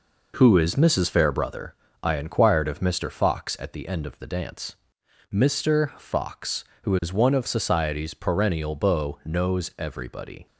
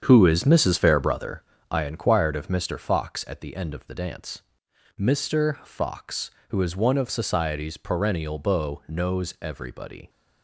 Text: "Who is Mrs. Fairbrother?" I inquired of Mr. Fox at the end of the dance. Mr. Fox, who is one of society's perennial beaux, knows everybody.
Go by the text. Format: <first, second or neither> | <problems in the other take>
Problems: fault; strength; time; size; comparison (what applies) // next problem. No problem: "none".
first | starts louder than the rest; strong; until 1.9 s; 7.5 dB